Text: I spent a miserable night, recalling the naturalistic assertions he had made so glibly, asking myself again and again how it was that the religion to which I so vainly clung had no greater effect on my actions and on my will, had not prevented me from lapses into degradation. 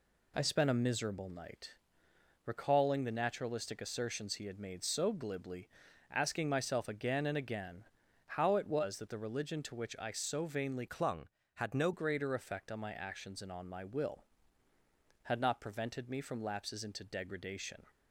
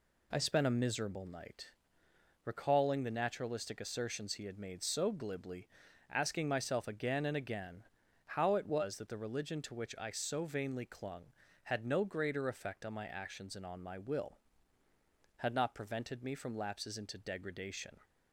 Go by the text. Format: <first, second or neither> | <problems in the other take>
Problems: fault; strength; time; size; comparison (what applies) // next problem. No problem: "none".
second | pauses between "again" and "how"; at 7.8 s; 0.42 s long; also in the second // changes voice from "clung" to "no"; from 10.8 to 11.9 s; 1.1 s long